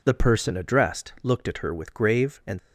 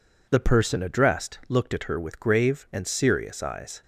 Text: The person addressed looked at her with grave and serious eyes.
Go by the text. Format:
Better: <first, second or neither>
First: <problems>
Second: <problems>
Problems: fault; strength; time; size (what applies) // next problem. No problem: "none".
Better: second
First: stops before "serious eyes"; at 2.5 s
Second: none